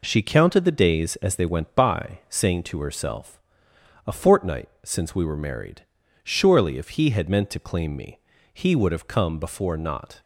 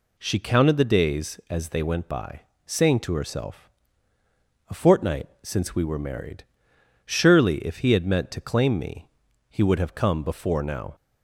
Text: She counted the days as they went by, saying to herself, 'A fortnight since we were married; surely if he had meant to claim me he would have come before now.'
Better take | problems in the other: second | pauses between "fortnight" and "since"; slight; at 4.6 s; 0.16 s long; slight in the second // pauses between "me" and "he"; slight; at 8.1 s; 0.34 s long; also in the second // says "not" for "now"; at 9.7 s

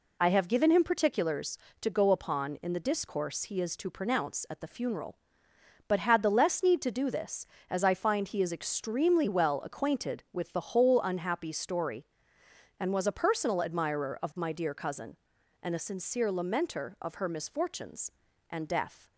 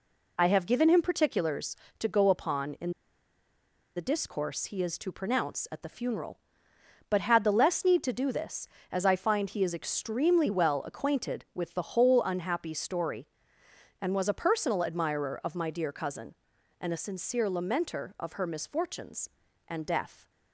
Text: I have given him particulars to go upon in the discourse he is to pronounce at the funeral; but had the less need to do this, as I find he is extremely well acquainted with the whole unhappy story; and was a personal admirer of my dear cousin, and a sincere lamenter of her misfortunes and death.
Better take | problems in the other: first | pauses between "in" and "the"; at 2.8 s; 1.0 s long

